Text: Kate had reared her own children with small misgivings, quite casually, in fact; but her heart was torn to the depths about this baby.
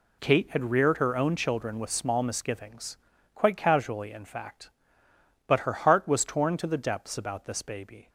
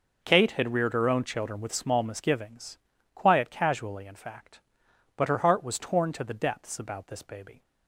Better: first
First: none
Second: says "quiet" for "quite"; at 3.1 s

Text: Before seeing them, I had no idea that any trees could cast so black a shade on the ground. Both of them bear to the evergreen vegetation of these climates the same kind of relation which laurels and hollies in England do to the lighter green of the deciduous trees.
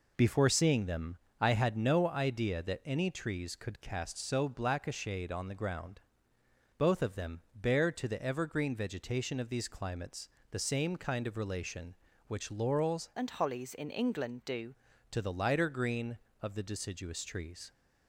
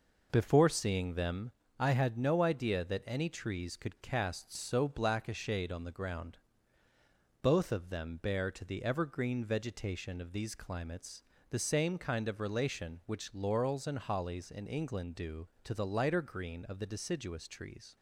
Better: second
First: pauses between "climates" and "the"; slight; at 10.2 s; 0.22 s long // changes voice from "and" to "do"; from 13.1 to 14.7 s; 1.6 s long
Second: pauses between "climates" and "the"; slight; at 11.2 s; 0.28 s long

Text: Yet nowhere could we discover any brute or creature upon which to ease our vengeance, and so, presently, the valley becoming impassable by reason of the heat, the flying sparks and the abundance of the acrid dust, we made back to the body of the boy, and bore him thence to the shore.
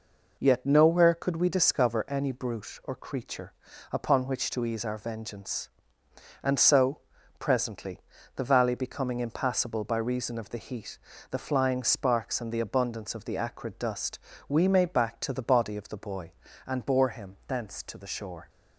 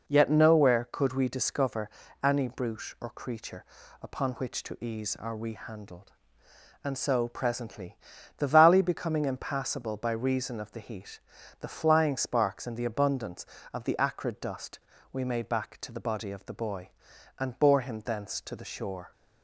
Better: first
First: pauses between "creature" and "upon"; at 3.5 s; 0.38 s long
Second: pauses between "discover" and "any"; slight; at 1.8 s; 0.34 s long // pauses between "creature" and "upon"; slight; at 3.6 s; 0.36 s long // says "rehandled" for "vengeance"; at 5.3 s

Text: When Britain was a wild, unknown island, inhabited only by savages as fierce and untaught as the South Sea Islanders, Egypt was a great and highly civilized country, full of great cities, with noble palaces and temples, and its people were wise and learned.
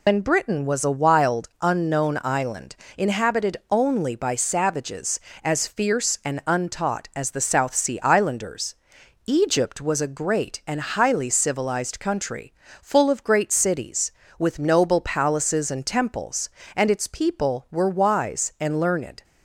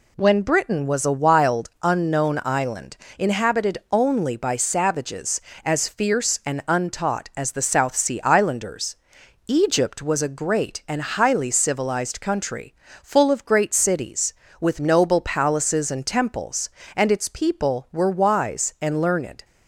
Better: second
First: loses the start of "When"; at 0.0 s; 115 ms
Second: none

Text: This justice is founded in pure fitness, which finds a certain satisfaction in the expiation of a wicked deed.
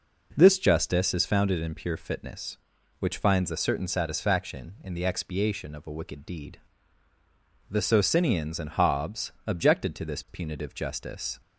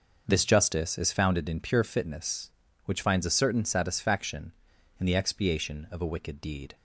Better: second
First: goes on to say "The Socinians and Hobbes objected to this punitive justice"; strong; from 7.6 s on; 3.7 s long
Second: none

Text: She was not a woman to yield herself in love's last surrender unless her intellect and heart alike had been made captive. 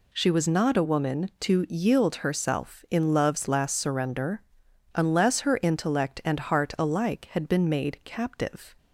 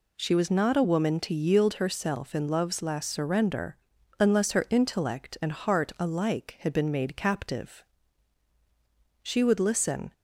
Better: first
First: pauses between "surrender" and "unless"; noticeable; at 4.4 s; 0.54 s long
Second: pauses between "surrender" and "unless"; at 3.7 s; 0.44 s long // goes on to say "She would listen"; noticeable; from 9.2 s on; 0.90 s long

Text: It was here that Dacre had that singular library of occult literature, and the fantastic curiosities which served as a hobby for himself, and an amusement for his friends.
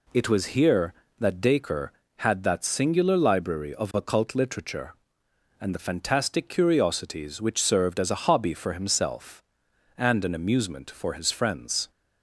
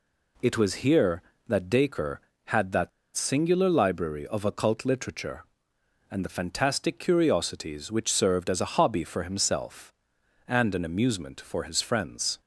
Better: first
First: none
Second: pauses between "that" and "singular"; slight; at 2.8 s; 0.26 s long

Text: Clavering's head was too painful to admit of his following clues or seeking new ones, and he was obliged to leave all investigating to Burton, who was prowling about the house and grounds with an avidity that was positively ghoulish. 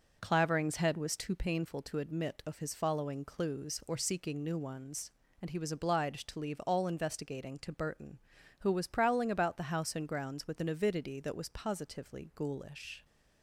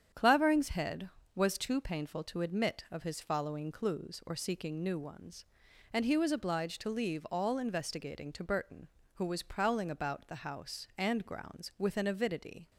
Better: first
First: none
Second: starts louder than the rest; strong; until 1.3 s; 8.5 dB // stops before "that was positively ghoulish"; at 12.7 s

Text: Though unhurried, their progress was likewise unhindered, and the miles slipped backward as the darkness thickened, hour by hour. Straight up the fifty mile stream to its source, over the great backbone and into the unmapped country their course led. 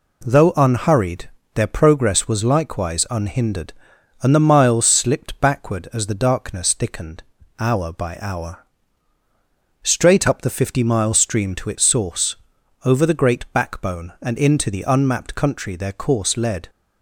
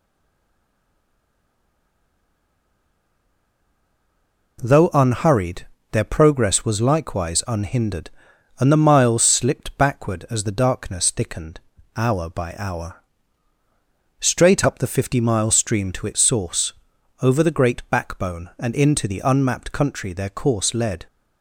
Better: first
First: none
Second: stays silent before the first word; strong; until 4.5 s; 4.5 s long

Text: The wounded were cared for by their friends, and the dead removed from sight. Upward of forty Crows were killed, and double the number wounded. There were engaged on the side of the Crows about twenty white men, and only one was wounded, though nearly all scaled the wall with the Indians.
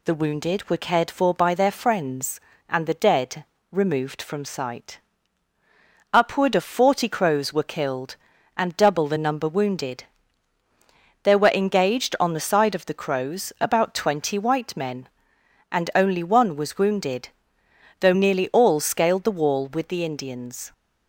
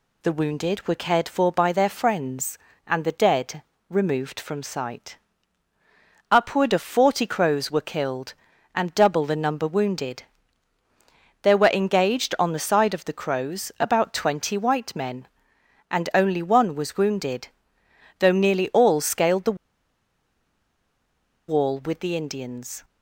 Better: first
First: pauses between "dead" and "removed"; slight; at 3.4 s; 0.26 s long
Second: pauses between "dead" and "removed"; slight; at 3.6 s; 0.26 s long // pauses between "the" and "wall"; strong; at 19.5 s; 1.9 s long

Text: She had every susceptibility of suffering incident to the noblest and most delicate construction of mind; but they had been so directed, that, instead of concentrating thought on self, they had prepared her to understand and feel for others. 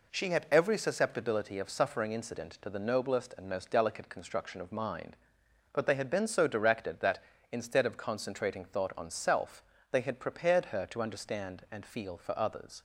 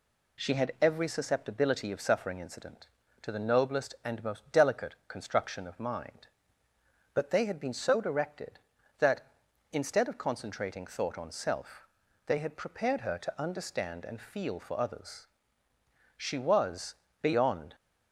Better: first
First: none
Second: goes on to say "She was beyond"; from 16.1 s on; 1.5 s long

